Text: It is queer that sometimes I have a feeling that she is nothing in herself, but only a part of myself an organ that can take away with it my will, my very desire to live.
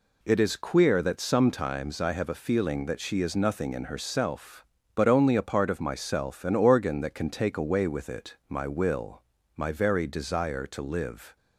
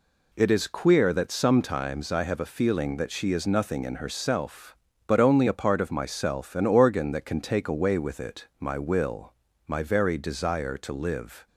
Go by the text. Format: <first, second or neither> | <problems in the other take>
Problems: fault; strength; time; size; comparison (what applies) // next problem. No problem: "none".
neither | none